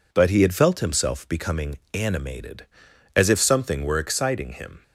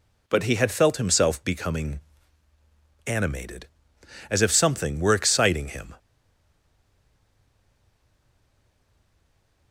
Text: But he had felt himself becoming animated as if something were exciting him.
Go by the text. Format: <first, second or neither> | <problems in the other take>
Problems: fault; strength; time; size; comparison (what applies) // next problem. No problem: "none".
first | pauses between "becoming" and "animated"; at 1.9 s; 1.0 s long // stays silent after the last word; strong; from 5.9 s on; 3.8 s long